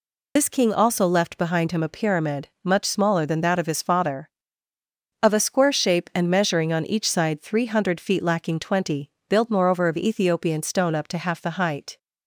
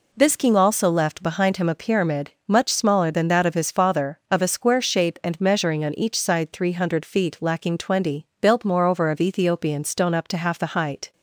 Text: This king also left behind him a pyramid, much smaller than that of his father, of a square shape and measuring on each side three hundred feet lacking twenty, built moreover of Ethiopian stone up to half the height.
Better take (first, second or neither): second